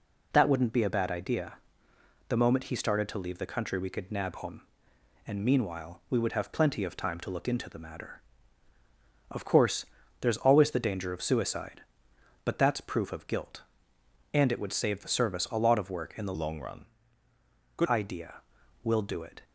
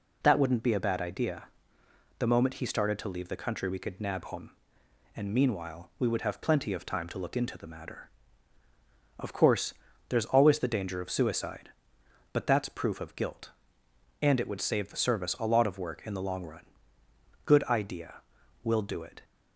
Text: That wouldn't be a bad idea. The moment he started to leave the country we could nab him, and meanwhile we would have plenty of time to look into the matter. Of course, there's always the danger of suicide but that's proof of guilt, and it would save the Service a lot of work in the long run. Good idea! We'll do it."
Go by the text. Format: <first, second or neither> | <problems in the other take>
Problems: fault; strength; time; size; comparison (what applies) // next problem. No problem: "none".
second | changes voice from "long" to "Good"; from 16.3 to 17.8 s; 1.5 s long